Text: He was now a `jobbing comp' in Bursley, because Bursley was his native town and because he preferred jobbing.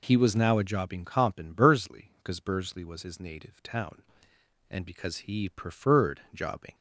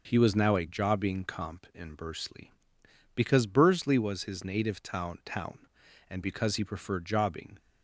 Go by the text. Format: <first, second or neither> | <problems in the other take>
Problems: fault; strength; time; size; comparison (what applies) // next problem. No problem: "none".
first | says "town" twice; at 5.2 s